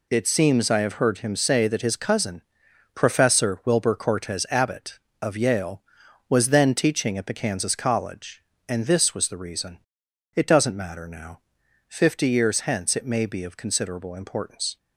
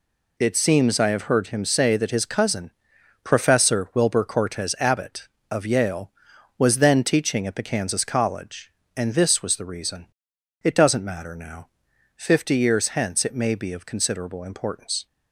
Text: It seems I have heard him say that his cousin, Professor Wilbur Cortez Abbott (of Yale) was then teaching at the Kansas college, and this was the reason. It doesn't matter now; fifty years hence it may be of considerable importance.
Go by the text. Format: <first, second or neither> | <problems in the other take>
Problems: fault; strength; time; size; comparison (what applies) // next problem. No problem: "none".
neither | none